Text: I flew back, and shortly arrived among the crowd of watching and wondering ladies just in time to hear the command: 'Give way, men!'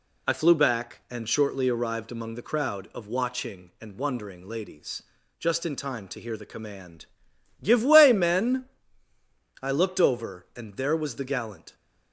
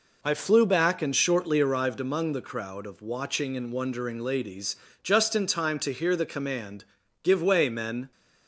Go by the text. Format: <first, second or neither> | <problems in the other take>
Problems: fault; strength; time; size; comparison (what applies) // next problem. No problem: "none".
second | pauses between "ladies" and "just"; slight; at 5.0 s; 0.36 s long; slight in the second // goes on to say "I looked over and there was the gallant"; strong; from 9.6 s on; 2.1 s long